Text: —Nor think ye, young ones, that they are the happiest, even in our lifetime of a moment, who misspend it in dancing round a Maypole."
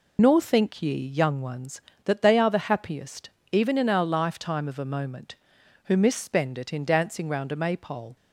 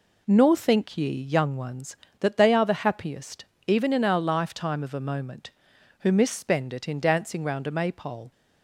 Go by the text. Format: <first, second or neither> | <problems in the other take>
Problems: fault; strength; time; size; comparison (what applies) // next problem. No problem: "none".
second | loses the start of "Nor"; at 0.1 s; 80 ms